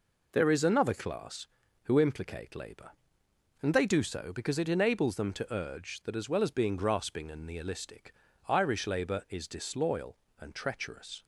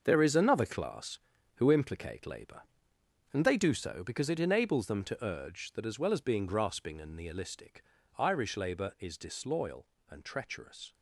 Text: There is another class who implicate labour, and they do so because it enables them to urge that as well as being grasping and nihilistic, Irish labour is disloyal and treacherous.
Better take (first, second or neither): first